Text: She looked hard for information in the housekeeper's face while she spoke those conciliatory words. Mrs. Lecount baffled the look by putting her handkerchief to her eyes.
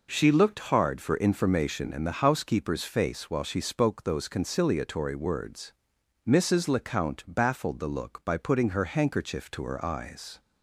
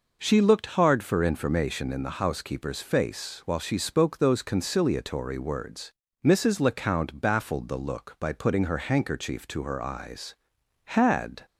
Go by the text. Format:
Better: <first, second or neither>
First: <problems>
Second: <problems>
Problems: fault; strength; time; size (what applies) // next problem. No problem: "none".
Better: first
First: none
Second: goes on to say "Had"; noticeable; from 10.8 s on; 0.62 s long